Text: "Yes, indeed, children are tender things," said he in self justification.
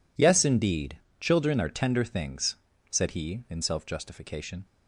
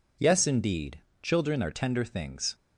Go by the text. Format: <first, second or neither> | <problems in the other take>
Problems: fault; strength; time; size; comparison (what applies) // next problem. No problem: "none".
first | stops before "said he in self justification"; at 2.5 s